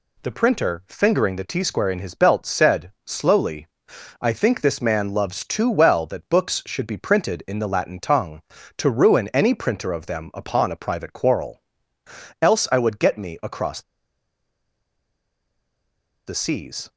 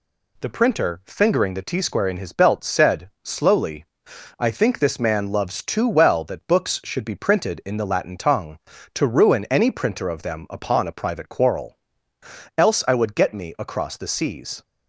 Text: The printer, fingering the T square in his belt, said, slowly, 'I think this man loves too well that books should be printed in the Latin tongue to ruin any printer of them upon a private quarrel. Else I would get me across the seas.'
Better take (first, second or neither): second